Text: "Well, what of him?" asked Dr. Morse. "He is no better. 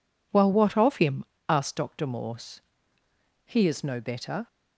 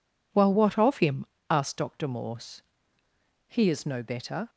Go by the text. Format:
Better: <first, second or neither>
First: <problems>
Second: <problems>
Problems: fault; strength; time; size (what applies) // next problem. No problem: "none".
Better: neither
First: none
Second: none